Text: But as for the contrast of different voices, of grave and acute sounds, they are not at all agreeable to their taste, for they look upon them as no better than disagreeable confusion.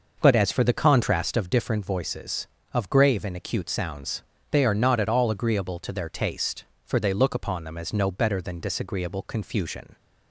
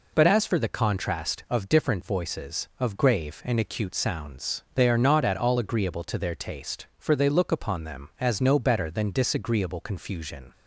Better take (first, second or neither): second